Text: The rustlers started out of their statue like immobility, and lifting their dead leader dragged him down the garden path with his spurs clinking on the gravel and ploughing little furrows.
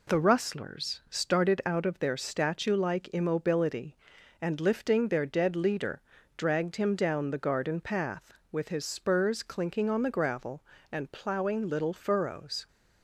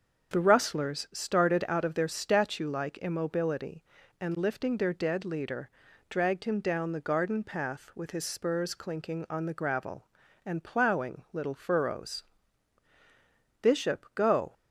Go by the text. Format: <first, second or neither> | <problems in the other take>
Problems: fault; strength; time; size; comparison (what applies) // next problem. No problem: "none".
first | starts louder than the rest; until 1.3 s; 6.5 dB // pauses between "leader" and "dragged"; at 5.6 s; 0.40 s long; also in the first // goes on to say "Bishop go"; noticeable; from 13.6 s on; 0.92 s long